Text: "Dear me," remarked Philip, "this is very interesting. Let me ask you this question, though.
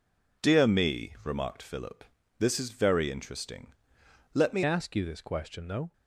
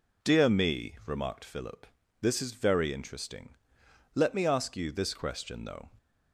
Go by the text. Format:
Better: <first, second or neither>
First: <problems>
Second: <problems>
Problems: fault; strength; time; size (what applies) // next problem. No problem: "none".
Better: second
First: changes voice at "ask"; from 4.6 s on; 1.3 s long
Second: none